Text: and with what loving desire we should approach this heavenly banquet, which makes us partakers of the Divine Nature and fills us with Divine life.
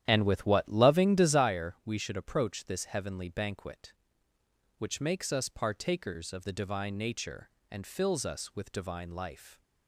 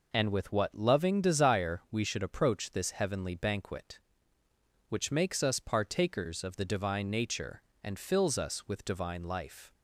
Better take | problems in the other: second | starts louder than the rest; strong; until 1.5 s; 11 dB

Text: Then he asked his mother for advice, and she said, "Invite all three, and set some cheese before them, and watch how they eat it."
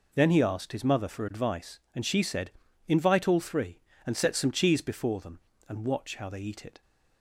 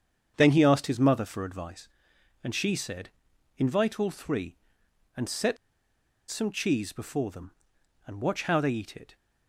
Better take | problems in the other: first | starts louder than the rest; strong; until 1.3 s; 7.5 dB // pauses between "set" and "some"; noticeable; at 5.5 s; 0.74 s long

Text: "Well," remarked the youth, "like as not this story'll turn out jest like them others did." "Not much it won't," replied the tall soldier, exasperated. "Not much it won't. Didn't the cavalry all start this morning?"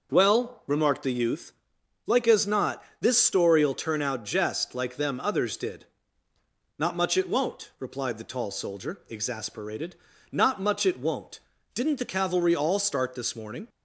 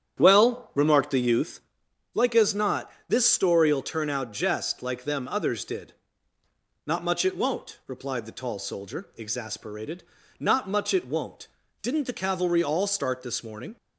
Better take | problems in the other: first | starts louder than the rest; strong; until 1.7 s; 9 dB // pauses between "not" and "this"; slight; at 2.9 s; 0.16 s long; slight in the first

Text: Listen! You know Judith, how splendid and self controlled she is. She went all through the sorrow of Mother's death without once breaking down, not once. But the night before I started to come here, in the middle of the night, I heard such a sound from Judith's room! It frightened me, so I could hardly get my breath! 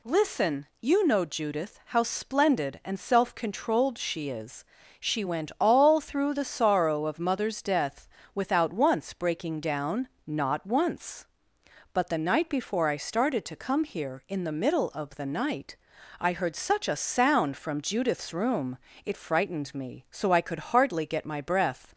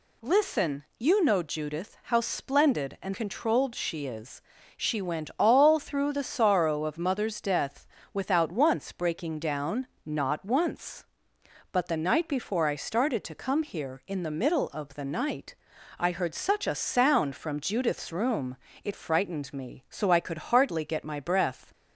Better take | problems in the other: first | skips "self"; at 3.1 s // pauses between "death" and "without"; slight; at 7.8 s; 0.26 s long; slight in the first

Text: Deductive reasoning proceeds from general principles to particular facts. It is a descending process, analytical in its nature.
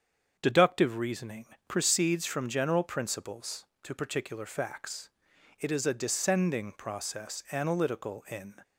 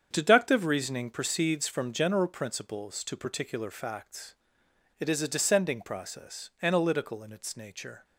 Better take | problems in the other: second | starts louder than the rest; strong; until 1.4 s; 7.5 dB; strong in the second // pauses between "reasoning" and "proceeds"; slight; at 1.4 s; 0.20 s long // stops before "its nature"; at 8.6 s

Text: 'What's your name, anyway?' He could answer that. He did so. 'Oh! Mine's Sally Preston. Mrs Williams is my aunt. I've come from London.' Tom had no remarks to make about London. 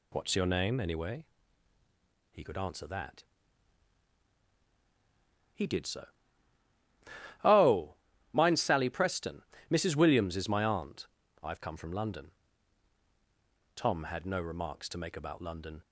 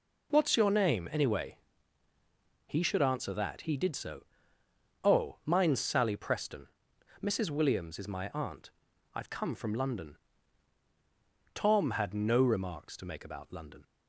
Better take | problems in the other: first | says "should" for "could"; at 2.8 s

